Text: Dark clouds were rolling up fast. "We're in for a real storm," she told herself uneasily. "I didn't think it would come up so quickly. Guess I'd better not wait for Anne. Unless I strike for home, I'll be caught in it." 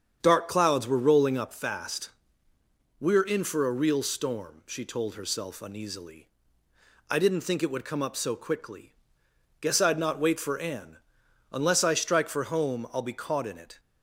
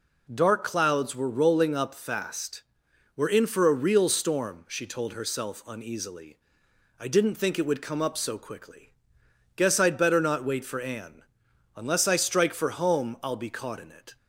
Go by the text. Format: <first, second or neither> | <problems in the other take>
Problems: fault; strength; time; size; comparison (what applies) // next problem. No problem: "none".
second | starts louder than the rest; strong; until 1.2 s; 7.5 dB // skips "better"; at 9.9 s